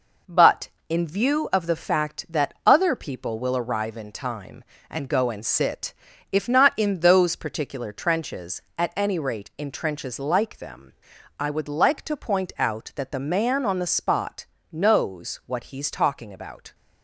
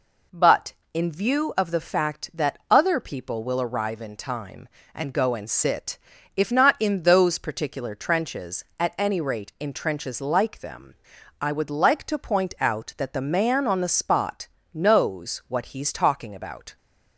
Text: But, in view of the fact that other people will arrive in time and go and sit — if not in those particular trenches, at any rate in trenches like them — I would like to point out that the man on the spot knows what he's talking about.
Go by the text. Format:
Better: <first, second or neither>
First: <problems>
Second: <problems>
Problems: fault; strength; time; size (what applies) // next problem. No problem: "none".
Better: second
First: gets quieter; noticeable; throughout; 4 dB // pauses between "spot" and "knows"; slight; at 14.4 s; 0.28 s long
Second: pauses between "spot" and "knows"; slight; at 14.4 s; 0.28 s long